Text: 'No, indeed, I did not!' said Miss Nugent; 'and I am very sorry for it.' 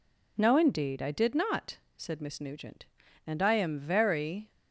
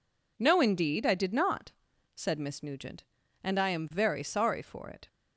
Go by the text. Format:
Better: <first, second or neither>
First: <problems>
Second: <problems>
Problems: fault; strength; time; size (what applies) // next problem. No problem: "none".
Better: second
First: stops before "sorry for it"; at 4.5 s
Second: none